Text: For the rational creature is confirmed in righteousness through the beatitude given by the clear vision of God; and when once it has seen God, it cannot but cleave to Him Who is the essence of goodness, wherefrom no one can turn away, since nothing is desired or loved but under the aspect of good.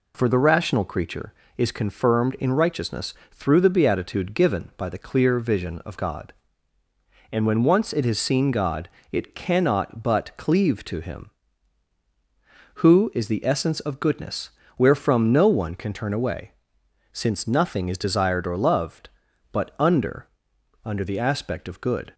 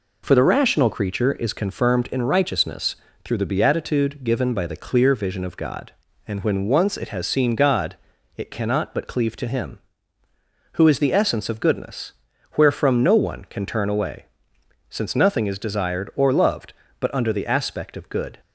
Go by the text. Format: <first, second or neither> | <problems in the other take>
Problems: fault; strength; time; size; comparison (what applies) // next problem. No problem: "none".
second | pauses between "righteousness" and "through"; slight; at 3.1 s; 0.20 s long; slight in the second // says "under" twice; at 20.8 s